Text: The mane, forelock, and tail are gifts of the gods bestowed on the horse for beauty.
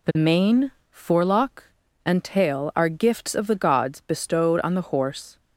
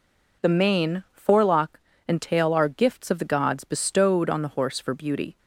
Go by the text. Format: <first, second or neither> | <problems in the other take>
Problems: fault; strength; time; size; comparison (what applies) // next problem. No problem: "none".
second | stops before "for beauty"; at 5.3 s